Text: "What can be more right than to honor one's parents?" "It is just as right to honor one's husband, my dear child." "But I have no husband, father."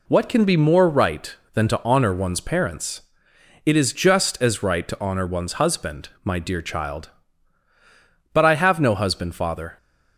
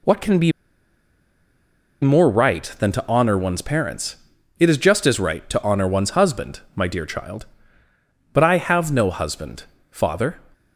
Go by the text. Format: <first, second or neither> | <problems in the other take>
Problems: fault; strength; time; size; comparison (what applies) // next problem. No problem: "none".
first | pauses between "be" and "more"; strong; at 0.5 s; 1.5 s long